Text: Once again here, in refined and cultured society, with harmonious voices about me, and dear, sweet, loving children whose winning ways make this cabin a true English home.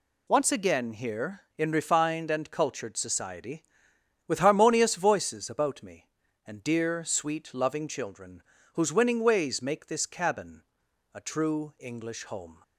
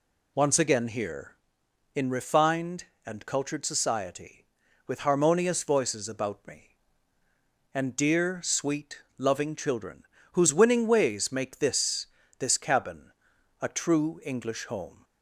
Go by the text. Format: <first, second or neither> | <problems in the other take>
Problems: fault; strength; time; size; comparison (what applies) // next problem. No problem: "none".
first | pauses between "children" and "whose"; slight; at 10.0 s; 0.30 s long; slight in the first // says "this" twice; at 12.3 s // pauses between "cabin" and "a"; noticeable; at 13.0 s; 0.50 s long; noticeable in the first